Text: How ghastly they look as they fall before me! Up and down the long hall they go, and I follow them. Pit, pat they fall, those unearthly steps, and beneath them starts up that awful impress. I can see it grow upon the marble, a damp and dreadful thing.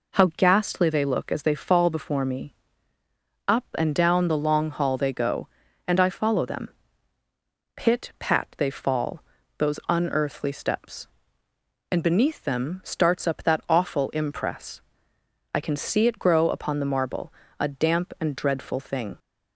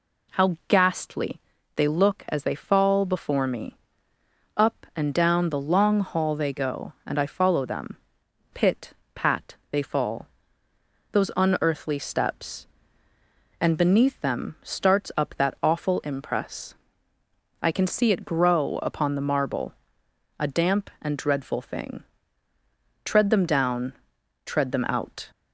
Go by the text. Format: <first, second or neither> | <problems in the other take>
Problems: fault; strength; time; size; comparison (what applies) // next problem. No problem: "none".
first | pauses between "ghastly" and "they"; slight; at 1.4 s; 0.36 s long // pauses between "pat" and "they"; slight; at 9.5 s; 0.16 s long // goes on to say "Tread them down tread them out"; strong; from 23.0 s on; 2.2 s long